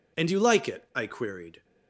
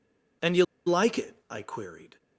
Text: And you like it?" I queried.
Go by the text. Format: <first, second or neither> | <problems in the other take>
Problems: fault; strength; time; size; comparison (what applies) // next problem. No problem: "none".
first | pauses between "you" and "like"; slight; at 0.6 s; 0.21 s long